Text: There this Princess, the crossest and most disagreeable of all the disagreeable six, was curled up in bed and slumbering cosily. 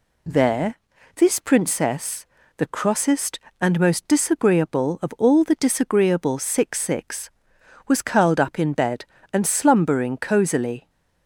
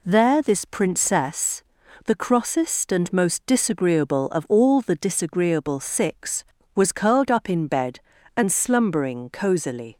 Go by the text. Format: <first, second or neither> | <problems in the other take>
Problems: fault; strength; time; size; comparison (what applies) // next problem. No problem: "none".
second | pauses between "There" and "this"; at 0.7 s; 0.40 s long // says "six" twice; at 6.8 s